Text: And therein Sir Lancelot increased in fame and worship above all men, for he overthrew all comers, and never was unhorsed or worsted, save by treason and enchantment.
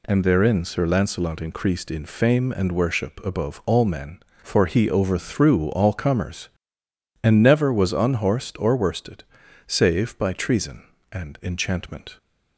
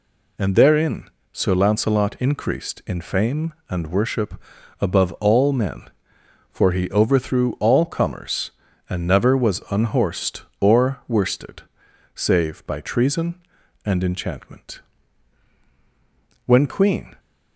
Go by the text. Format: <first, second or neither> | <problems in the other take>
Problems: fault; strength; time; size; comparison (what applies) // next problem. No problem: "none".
first | pauses between "therein" and "Sir"; slight; at 1.0 s; 0.22 s long // pauses between "worship" and "above"; at 4.3 s; 0.42 s long // goes on to say "When Queen"; noticeable; from 16.4 s on; 0.70 s long